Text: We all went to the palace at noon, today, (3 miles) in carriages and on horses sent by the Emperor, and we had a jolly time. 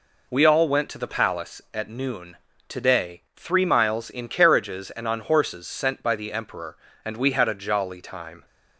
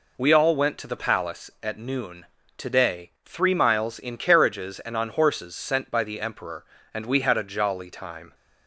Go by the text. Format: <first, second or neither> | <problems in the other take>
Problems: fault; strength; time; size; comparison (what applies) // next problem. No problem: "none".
neither | none